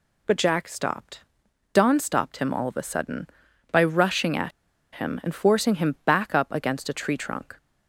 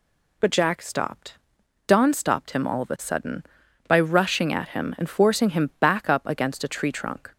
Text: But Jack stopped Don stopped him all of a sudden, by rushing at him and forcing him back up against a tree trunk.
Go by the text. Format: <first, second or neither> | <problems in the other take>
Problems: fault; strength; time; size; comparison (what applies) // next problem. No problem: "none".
second | pauses between "stopped" and "Don"; noticeable; at 1.1 s; 0.54 s long; noticeable in the second // pauses between "at" and "him"; at 4.5 s; 0.43 s long